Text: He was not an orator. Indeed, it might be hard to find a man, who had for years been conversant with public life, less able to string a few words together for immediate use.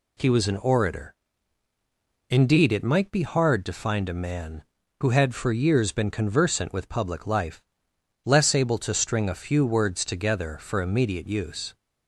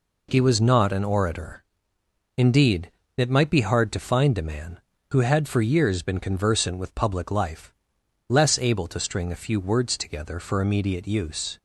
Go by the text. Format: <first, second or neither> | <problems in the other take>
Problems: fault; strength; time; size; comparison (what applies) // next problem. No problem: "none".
second | skips "not"; at 0.4 s